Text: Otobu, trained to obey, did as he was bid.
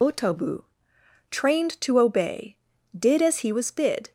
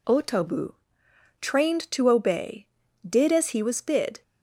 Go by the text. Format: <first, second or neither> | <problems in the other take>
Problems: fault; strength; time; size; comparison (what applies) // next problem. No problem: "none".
second | loses the start of "Otobu"; at 0.0 s; 50 ms